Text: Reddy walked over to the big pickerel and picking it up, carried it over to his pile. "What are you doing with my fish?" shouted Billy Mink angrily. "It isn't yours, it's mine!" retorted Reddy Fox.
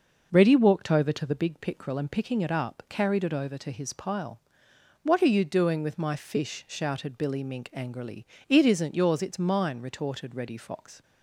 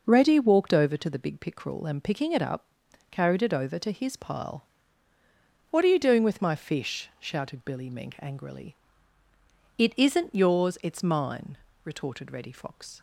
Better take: neither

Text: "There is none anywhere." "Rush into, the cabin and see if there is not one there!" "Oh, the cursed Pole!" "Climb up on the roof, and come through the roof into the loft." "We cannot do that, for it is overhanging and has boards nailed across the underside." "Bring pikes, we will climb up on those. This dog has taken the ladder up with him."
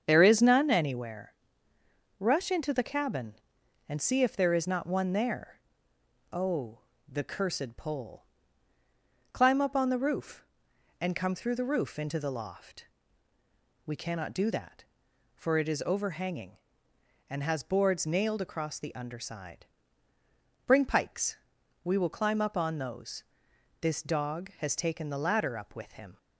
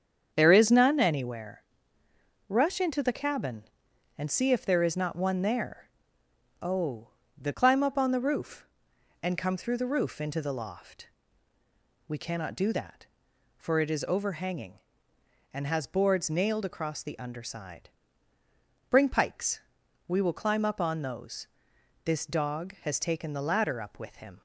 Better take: first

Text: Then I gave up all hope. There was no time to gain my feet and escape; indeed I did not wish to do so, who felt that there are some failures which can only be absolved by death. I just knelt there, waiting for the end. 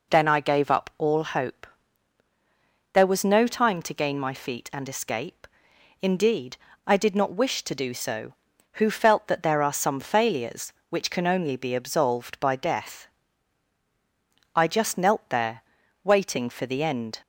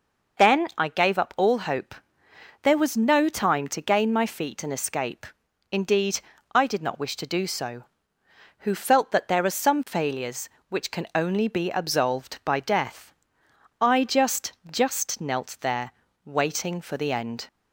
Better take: first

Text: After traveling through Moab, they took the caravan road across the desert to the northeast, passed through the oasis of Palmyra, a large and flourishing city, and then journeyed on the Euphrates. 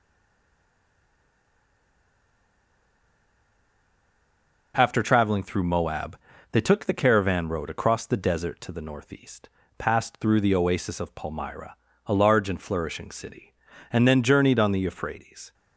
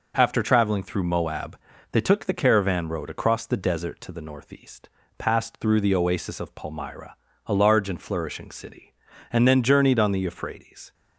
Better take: second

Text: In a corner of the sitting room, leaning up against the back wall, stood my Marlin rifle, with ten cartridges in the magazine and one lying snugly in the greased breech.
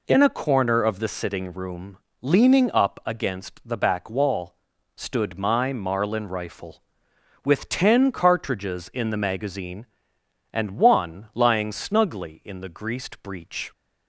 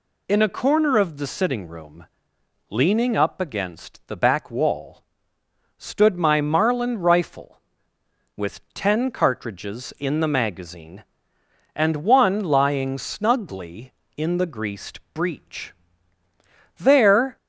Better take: first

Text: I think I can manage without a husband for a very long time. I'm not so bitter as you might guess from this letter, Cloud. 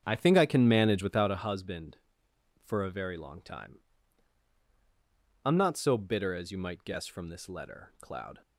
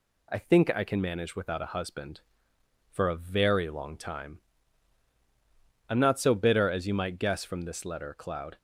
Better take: second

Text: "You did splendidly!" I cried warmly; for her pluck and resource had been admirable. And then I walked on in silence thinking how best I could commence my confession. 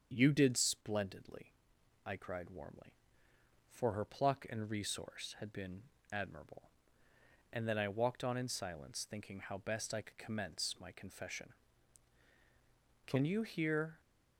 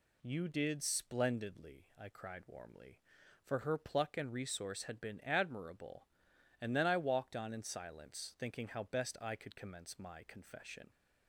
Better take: second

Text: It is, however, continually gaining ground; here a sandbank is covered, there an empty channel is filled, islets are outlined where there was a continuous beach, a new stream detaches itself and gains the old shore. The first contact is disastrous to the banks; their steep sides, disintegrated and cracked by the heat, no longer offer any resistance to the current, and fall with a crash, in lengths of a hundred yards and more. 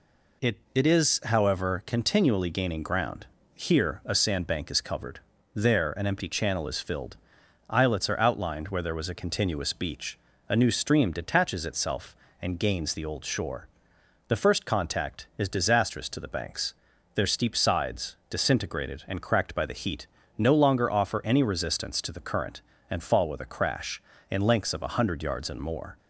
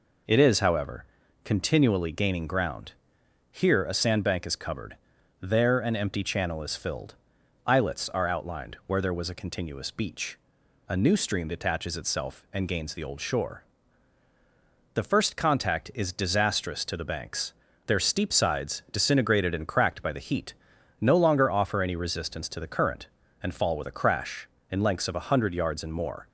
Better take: second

